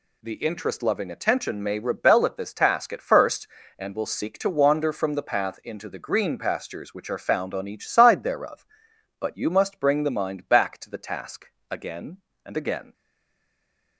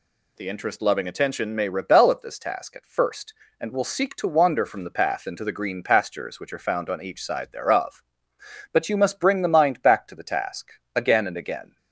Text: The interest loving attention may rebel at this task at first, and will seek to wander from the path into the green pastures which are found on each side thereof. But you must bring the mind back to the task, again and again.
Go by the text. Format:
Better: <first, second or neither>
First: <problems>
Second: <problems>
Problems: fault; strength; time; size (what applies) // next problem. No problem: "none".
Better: second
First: stays silent after the last word; from 12.9 s on; 1.0 s long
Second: none